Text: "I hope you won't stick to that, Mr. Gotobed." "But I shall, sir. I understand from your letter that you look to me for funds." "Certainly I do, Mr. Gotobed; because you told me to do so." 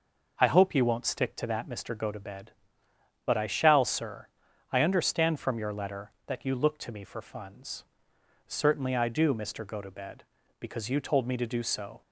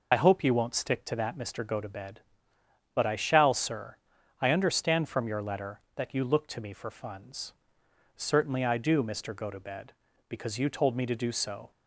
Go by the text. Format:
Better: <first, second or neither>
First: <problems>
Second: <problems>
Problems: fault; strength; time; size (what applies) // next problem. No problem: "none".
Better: first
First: none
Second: loses the start of "I"; at 0.1 s; 45 ms